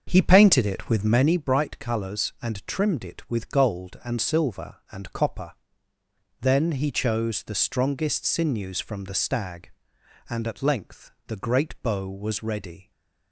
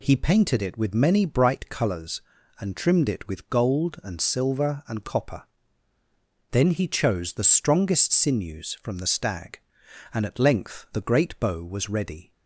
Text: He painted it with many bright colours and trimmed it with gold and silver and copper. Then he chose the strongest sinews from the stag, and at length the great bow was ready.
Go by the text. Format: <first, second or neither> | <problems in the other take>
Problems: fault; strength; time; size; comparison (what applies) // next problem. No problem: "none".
second | starts louder than the rest; until 1.3 s; 6.5 dB // pauses between "length" and "the"; slight; at 11.1 s; 0.16 s long